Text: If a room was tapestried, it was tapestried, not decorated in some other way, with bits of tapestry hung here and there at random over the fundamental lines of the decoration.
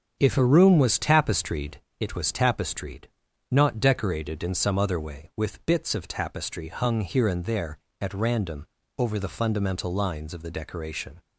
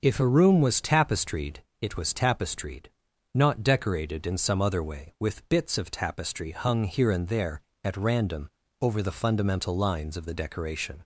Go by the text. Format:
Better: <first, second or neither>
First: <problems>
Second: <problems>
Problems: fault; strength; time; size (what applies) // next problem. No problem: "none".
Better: second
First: gets quieter; throughout; 6.5 dB // starts louder than the rest; strong; until 1.2 s; 7.5 dB // pauses between "random" and "over"; slight; at 8.6 s; 0.32 s long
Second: starts louder than the rest; until 1.0 s; 6 dB // pauses between "random" and "over"; slight; at 8.4 s; 0.32 s long